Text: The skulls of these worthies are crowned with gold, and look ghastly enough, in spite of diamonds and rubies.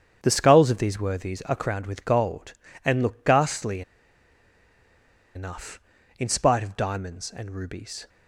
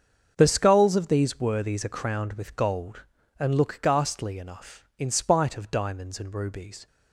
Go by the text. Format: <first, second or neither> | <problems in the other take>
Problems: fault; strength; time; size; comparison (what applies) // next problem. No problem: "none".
second | starts louder than the rest; strong; until 1.2 s; 8 dB; also in the second // pauses between "ghastly" and "enough"; strong; at 3.8 s; 1.5 s long